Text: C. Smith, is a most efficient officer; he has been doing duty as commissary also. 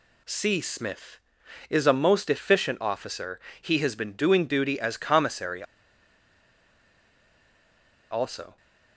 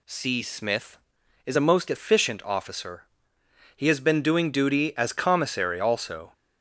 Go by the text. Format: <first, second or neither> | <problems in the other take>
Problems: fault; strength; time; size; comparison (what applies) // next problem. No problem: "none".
second | pauses between "commissary" and "also"; strong; at 5.6 s; 2.4 s long